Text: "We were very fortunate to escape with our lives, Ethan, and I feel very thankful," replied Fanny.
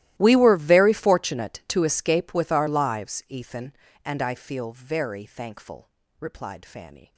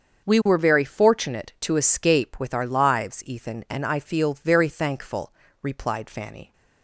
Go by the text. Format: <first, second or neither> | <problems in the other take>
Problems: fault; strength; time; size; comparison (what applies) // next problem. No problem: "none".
second | gets quieter; strong; throughout; 24 dB // starts louder than the rest; strong; until 1.1 s; 15 dB; also in the second